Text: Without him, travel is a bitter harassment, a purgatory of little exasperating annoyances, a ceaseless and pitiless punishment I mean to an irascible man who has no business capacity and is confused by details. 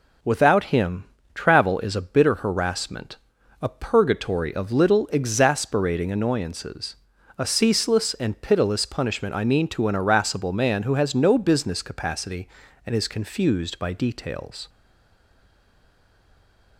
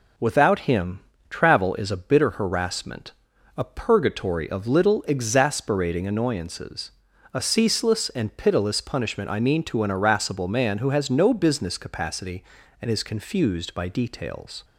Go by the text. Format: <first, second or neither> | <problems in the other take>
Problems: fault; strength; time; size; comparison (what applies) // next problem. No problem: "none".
second | stays silent after the last word; from 14.6 s on; 2.1 s long